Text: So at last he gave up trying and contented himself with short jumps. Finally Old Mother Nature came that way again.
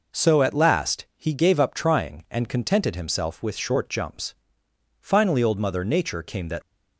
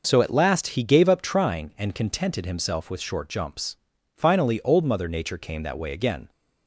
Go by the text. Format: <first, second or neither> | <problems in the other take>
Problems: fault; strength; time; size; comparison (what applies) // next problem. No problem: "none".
second | stops before "way again"; at 6.6 s